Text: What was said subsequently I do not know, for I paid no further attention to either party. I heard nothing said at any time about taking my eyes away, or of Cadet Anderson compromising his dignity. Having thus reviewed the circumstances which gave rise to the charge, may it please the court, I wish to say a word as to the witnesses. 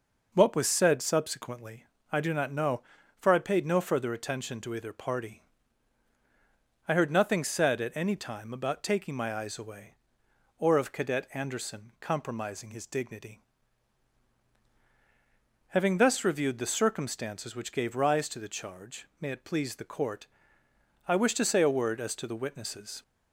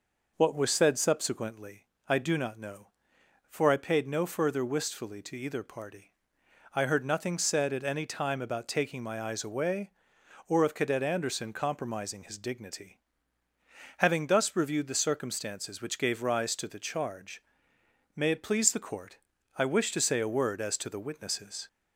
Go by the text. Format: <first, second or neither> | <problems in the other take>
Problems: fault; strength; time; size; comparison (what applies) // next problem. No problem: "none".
first | pauses between "subsequently" and "I"; slight; at 1.8 s; 0.24 s long; slight in the first // says "wistfully" for "attention"; at 4.6 s